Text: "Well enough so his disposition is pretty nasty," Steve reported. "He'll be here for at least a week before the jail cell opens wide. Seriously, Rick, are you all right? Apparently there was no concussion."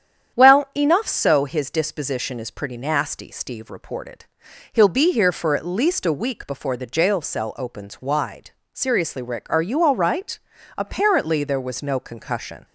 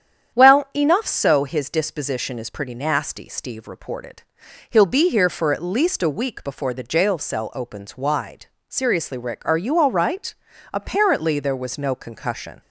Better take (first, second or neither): neither